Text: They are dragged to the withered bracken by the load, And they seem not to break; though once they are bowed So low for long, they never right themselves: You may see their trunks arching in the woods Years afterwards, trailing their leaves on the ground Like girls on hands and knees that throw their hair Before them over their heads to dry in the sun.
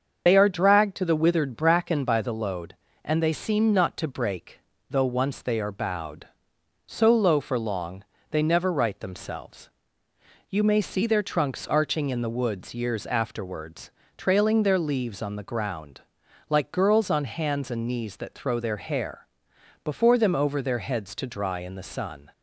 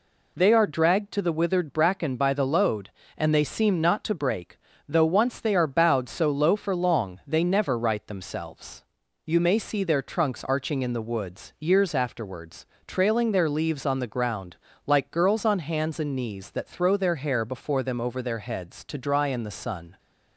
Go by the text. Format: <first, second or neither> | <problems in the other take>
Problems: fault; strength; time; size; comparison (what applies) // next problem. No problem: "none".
second | loses the start of "They"; at 0.2 s; 60 ms // starts louder than the rest; until 1.2 s; 7 dB // pauses between "ground" and "Like"; noticeable; at 15.9 s; 0.50 s long; slight in the second // pauses between "hair" and "Before"; noticeable; at 19.2 s; 0.56 s long